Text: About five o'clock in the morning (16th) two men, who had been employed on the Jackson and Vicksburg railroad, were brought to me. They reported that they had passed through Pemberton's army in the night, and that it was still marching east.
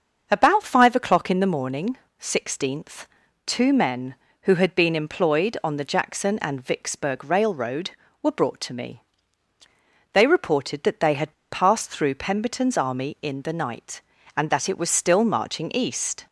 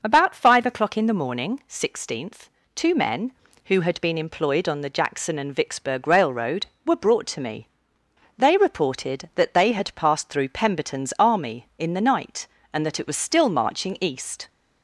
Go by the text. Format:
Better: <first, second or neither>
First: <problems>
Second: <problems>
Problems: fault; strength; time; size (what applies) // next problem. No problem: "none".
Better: second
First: starts louder than the rest; until 1.3 s; 6.5 dB // pauses between "had" and "passed"; slight; at 11.3 s; 0.19 s long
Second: none